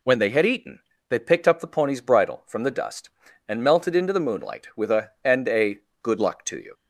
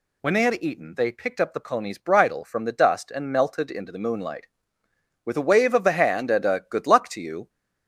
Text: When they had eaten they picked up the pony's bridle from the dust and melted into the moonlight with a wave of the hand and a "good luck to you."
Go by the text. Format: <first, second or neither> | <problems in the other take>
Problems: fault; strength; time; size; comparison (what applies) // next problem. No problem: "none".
second | pauses between "eaten" and "they"; slight; at 0.7 s; 0.30 s long // skips "wave of the hand"; at 5.1 s // pauses between "a" and "good"; slight; at 5.7 s; 0.24 s long